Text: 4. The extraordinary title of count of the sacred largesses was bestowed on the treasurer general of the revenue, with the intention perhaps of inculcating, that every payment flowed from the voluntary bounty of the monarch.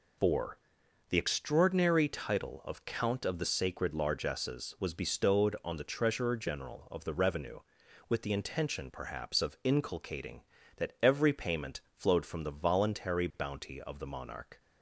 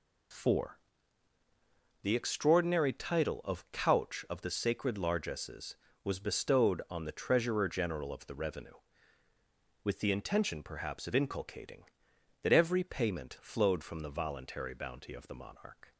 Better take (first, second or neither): first